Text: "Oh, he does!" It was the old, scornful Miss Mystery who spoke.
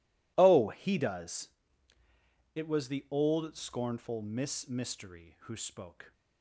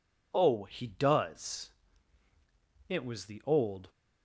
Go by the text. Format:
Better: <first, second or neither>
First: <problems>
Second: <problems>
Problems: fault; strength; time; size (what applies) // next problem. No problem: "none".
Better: first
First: none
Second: stops before "scornful Miss Mystery who spoke"; at 3.8 s